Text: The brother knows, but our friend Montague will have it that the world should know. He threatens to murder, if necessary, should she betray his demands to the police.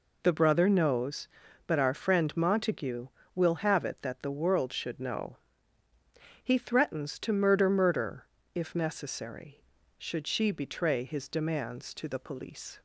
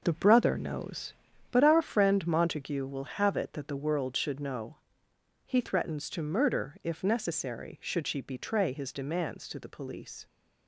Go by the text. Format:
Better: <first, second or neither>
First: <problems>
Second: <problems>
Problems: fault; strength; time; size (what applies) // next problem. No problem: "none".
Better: second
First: says "murder" twice; at 7.6 s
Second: none